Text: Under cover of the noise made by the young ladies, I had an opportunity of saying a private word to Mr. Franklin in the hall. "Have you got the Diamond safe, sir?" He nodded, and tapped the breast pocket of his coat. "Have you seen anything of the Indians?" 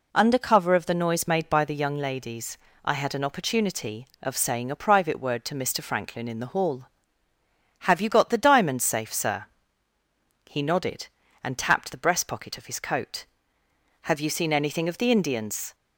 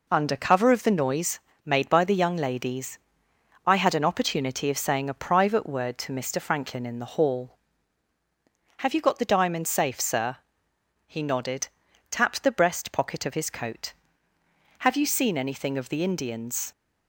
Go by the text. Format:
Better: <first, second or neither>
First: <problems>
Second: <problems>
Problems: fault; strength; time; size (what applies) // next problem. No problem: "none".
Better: first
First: none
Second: pauses between "noise" and "made"; slight; at 1.3 s; 0.26 s long // skips "and"; at 11.8 s